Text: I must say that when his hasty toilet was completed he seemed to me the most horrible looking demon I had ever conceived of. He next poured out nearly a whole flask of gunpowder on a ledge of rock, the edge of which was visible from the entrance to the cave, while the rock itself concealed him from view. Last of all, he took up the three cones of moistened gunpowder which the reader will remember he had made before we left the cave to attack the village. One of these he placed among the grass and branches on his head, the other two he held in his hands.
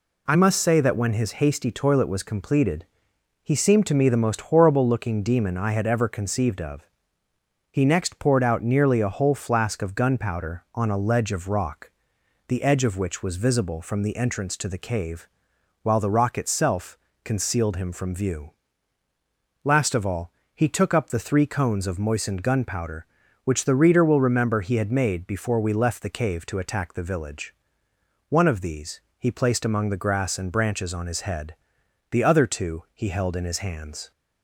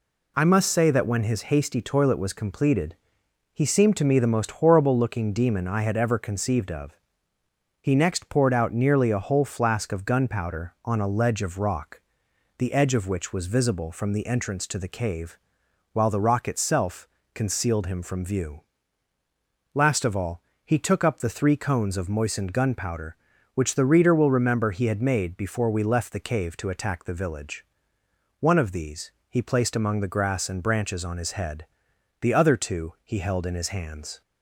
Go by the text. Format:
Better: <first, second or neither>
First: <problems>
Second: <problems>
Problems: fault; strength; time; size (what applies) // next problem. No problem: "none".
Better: neither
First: pauses between "completed" and "he"; noticeable; at 2.8 s; 0.56 s long // pauses between "itself" and "concealed"; slight; at 16.9 s; 0.28 s long // pauses between "these" and "he"; slight; at 29.0 s; 0.18 s long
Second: pauses between "completed" and "he"; noticeable; at 2.9 s; 0.56 s long // pauses between "itself" and "concealed"; slight; at 17.0 s; 0.28 s long // pauses between "these" and "he"; slight; at 29.1 s; 0.18 s long